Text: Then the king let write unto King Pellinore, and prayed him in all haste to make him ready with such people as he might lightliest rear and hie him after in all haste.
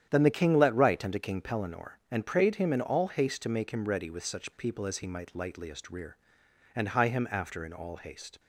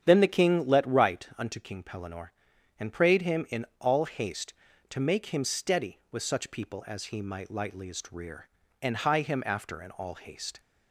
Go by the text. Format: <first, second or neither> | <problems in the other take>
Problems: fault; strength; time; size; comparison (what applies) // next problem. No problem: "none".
first | starts louder than the rest; strong; until 1.0 s; 8.5 dB; strong in the first // says "steady" for "ready"; at 5.4 s